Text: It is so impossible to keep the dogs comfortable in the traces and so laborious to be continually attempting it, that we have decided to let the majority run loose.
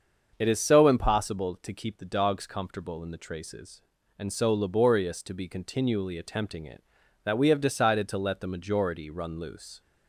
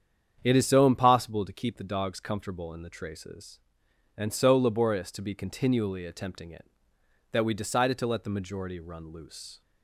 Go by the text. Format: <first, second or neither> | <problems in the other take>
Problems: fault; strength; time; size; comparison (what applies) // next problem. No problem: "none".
first | starts louder than the rest; strong; until 1.4 s; 8.5 dB; also in the first // skips "have"; at 7.5 s